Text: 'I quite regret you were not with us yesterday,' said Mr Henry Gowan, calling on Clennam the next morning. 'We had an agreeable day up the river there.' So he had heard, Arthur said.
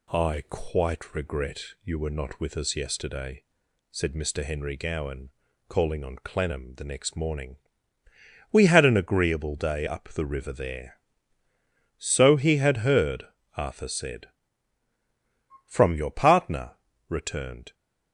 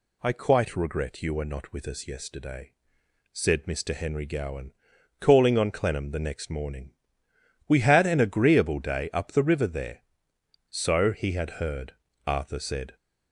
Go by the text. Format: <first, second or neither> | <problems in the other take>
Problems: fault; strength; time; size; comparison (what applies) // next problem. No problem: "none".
second | pauses between "regret" and "you"; slight; at 1.6 s; 0.24 s long // goes on to say "From your partner returned"; strong; from 15.6 s on; 2.0 s long